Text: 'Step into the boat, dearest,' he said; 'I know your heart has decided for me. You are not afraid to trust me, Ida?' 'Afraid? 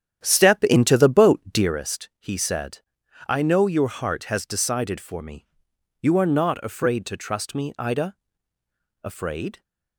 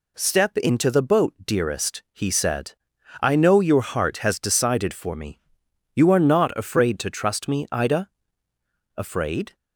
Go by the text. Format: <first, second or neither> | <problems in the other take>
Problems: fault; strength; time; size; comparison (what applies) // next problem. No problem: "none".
second | starts louder than the rest; strong; until 1.8 s; 9.5 dB